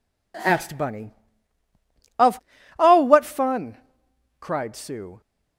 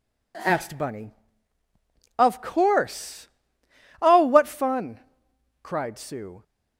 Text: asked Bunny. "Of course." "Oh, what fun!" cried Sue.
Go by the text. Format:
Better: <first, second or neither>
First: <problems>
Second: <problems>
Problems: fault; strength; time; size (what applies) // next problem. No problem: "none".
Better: second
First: skips "course"; at 2.5 s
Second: none